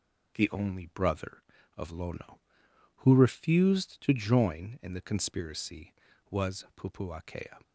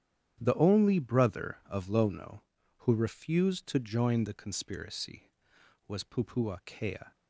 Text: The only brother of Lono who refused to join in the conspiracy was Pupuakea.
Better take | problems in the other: first | starts louder than the rest; strong; until 1.4 s; 10 dB // skips "in"; at 4.2 s

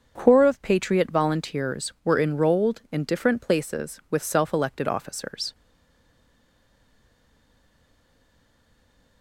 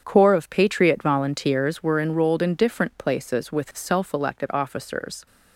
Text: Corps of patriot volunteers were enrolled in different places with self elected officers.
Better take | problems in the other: second | starts louder than the rest; until 1.1 s; 6.5 dB; strong in the second // stays silent after the last word; strong; from 5.5 s on; 3.7 s long

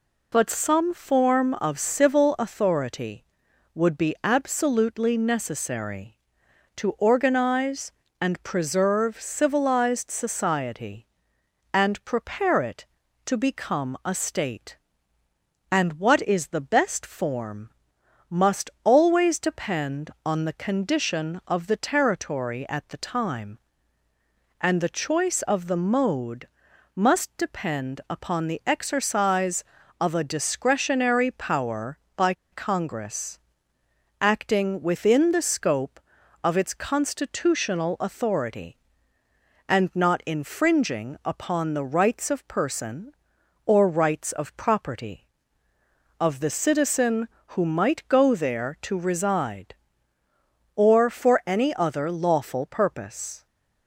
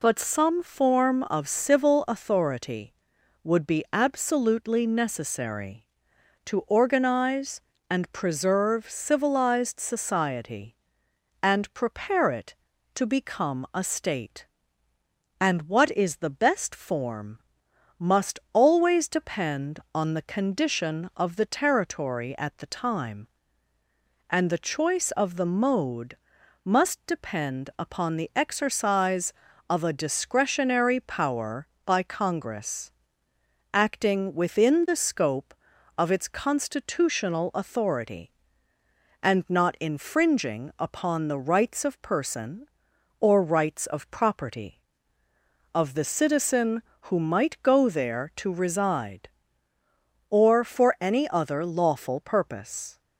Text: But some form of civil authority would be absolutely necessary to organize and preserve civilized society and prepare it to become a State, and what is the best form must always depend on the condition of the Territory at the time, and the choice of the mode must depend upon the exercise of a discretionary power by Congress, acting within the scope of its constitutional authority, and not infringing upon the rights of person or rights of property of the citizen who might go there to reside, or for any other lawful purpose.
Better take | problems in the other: second | pauses between "form" and "must"; noticeable; at 17.6 s; 0.58 s long; noticeable in the second // pauses between "mode" and "must"; noticeable; at 26.4 s; 0.48 s long; noticeable in the second // pauses between "by" and "Congress"; slight; at 32.3 s; 0.18 s long

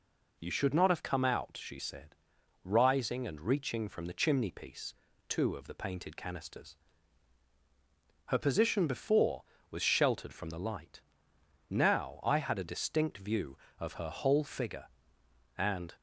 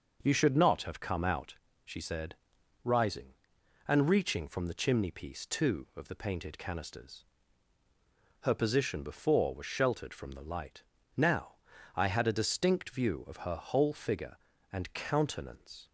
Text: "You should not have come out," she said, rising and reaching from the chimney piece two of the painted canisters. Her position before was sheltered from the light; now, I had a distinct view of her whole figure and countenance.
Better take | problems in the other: second | pauses between "piece" and "two"; slight; at 4.9 s; 0.34 s long // stops before "countenance"; at 15.9 s

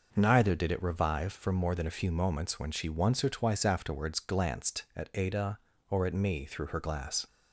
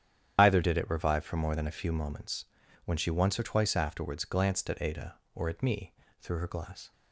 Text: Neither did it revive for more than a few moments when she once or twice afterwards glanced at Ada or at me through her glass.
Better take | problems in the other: first | loses the start of "Neither"; at 0.3 s; 115 ms // starts louder than the rest; strong; until 1.3 s; 10 dB // pauses between "moments" and "when"; at 2.4 s; 0.40 s long // pauses between "me" and "through"; slight; at 5.9 s; 0.26 s long

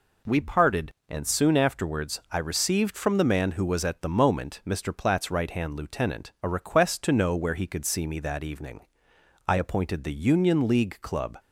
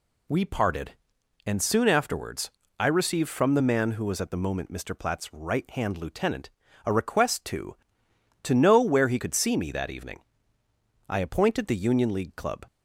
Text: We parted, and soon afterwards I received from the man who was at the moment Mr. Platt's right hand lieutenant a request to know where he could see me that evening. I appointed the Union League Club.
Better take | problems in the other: first | pauses between "afterwards" and "I"; slight; at 2.4 s; 0.28 s long // pauses between "lieutenant" and "a"; slight; at 6.5 s; 0.34 s long // says "to" twice; at 8.4 s

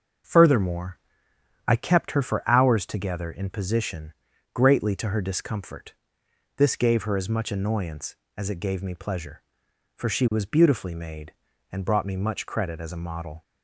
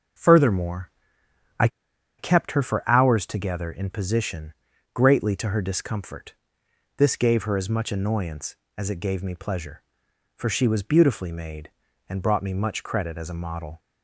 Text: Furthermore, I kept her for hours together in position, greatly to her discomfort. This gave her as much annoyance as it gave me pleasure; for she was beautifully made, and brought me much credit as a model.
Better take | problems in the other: first | starts louder than the rest; until 2.3 s; 6.5 dB; also in the first // pauses between "I" and "kept"; noticeable; at 1.6 s; 0.51 s long

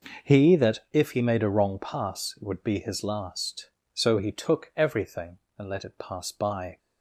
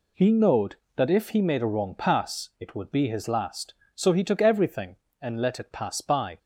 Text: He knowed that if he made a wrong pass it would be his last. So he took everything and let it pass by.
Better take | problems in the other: second | skips "knowed"; at 0.5 s

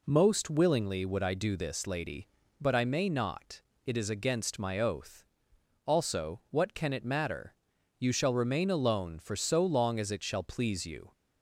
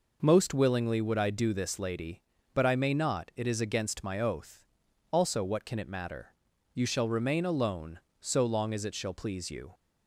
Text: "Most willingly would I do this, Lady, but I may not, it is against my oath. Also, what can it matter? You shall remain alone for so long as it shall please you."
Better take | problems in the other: first | skips "for"; at 8.0 s

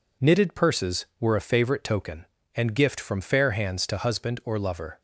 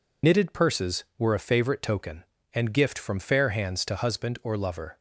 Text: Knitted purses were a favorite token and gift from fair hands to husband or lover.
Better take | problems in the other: first | loses the start of "Knitted"; at 0.2 s; 50 ms

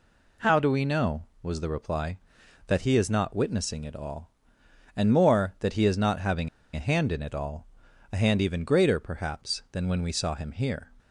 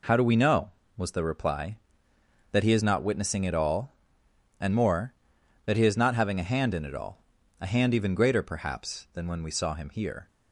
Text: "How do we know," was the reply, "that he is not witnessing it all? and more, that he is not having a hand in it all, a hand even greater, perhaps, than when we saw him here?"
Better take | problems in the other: second | pauses between "having" and "a"; slight; at 6.4 s; 0.27 s long

